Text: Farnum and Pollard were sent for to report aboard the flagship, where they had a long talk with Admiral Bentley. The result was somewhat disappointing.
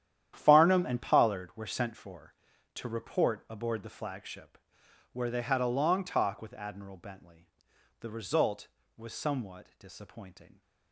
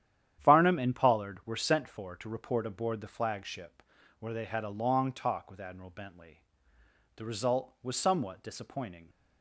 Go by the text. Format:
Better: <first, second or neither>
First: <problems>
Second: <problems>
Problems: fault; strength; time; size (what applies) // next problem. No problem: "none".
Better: second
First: gets quieter; strong; throughout; 13 dB // starts louder than the rest; strong; until 1.3 s; 10.5 dB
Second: starts louder than the rest; strong; until 1.4 s; 10.5 dB